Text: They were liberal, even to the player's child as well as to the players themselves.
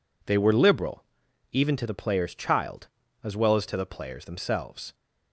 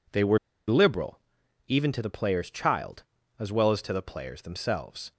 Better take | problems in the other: first | pauses between "were" and "liberal"; slight; at 0.3 s; 0.29 s long

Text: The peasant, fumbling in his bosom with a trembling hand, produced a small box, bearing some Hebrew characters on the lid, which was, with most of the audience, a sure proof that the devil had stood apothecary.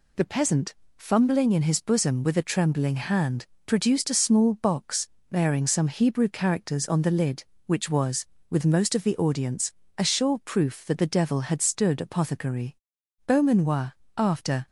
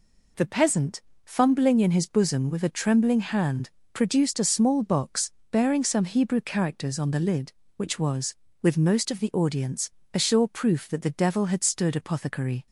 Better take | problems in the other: second | goes on to say "Beaumanoir after"; from 13.2 s on; 1.4 s long

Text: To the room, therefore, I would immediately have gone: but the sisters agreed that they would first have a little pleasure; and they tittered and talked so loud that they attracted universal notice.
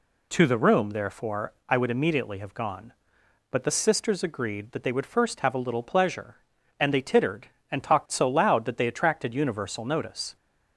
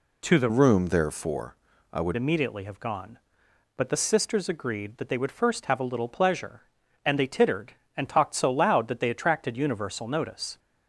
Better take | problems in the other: first | changes voice from "room" to "would"; from 0.4 to 2.1 s; 1.7 s long

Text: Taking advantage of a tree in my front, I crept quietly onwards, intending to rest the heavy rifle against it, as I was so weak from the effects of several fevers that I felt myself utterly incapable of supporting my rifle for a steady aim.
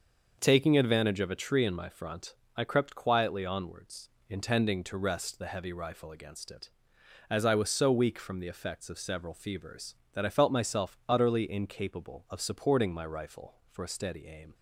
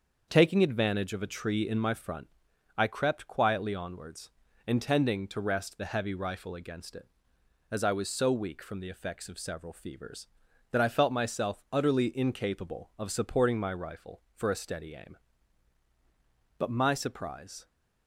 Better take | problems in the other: first | starts louder than the rest; until 1.3 s; 6.5 dB; also in the first // goes on to say "But my surprise"; noticeable; from 16.5 s on; 1.1 s long

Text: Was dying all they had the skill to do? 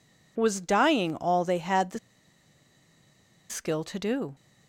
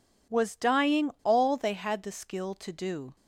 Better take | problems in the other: second | pauses between "the" and "skill"; strong; at 1.9 s; 1.5 s long

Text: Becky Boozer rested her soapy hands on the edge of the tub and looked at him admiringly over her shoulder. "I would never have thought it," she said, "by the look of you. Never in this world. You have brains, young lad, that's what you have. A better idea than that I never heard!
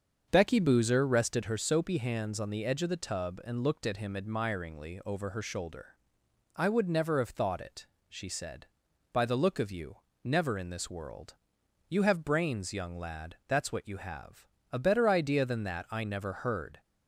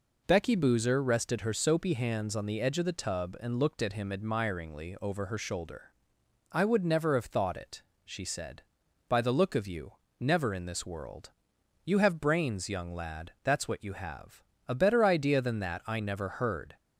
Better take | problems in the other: second | starts louder than the rest; until 1.6 s; 7 dB

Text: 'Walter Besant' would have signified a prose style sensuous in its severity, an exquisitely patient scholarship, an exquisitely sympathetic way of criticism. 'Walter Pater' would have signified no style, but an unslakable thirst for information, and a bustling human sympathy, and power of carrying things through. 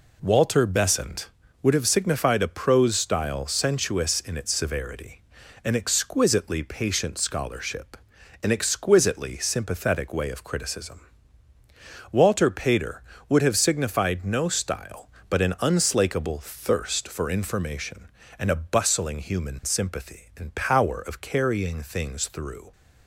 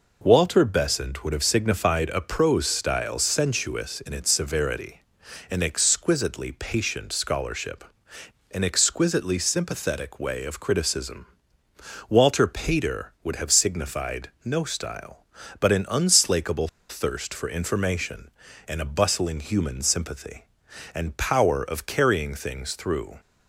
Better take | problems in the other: first | pauses between "unslakable" and "thirst"; slight; at 16.6 s; 0.21 s long

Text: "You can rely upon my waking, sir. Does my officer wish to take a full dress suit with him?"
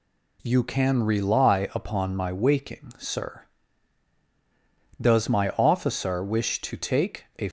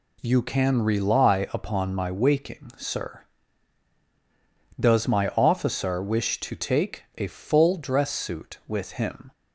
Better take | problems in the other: second | stops before "full dress suit with him"; at 7.4 s

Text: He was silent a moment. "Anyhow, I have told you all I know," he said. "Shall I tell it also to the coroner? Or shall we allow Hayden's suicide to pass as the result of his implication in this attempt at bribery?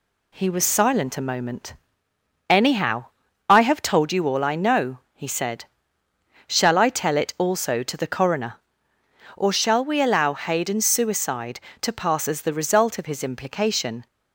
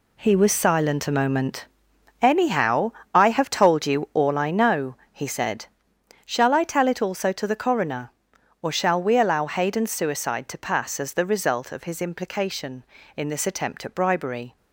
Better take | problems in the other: second | stops before "in this attempt at bribery"; at 14.0 s

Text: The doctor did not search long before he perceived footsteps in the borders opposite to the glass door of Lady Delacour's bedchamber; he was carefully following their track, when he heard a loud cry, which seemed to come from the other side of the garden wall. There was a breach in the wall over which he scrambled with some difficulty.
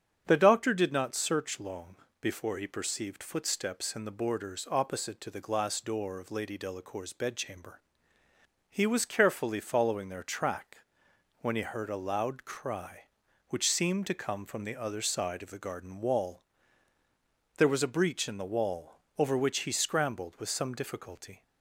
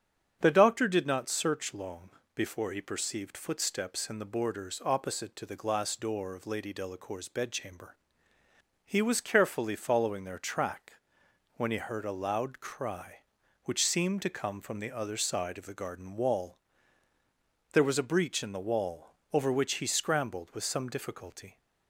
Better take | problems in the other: neither | starts louder than the rest; strong; the same in both // pauses between "long" and "before"; slight; the same in both // pauses between "wall" and "over"; slight; the same in both

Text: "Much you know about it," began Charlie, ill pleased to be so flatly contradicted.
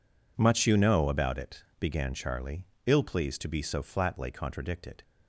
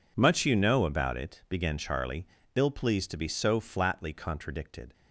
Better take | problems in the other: neither | none

